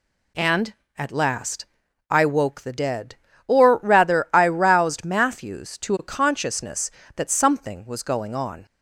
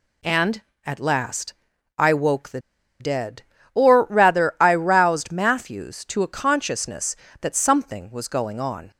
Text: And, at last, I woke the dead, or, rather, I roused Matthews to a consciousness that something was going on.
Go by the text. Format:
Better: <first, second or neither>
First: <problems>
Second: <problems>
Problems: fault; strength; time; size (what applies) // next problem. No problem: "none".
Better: first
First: none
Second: pauses between "the" and "dead"; at 2.5 s; 0.40 s long